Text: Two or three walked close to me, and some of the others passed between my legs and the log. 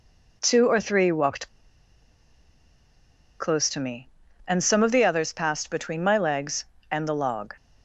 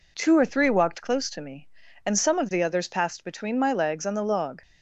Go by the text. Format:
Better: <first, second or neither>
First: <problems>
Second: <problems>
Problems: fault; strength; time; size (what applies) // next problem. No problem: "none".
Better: second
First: pauses between "walked" and "close"; strong; at 1.4 s; 1.9 s long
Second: none